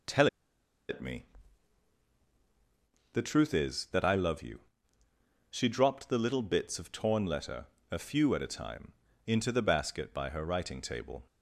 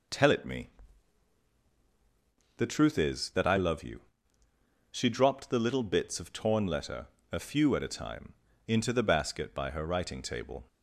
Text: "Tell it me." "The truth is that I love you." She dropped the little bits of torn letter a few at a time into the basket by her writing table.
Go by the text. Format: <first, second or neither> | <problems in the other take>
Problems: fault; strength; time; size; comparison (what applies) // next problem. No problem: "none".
second | pauses between "Tell" and "it"; noticeable; at 0.2 s; 0.62 s long // pauses between "letter" and "a"; slight; at 7.6 s; 0.24 s long; slight in the second // pauses between "time" and "into"; slight; at 8.9 s; 0.34 s long; slight in the second